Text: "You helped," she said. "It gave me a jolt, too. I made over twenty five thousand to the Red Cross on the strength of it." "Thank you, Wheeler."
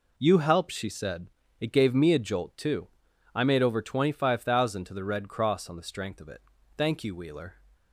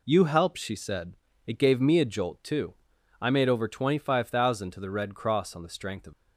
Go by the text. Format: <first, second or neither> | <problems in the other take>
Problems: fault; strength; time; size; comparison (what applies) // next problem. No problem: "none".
first | stops before "it Thank you Wheeler"; at 6.1 s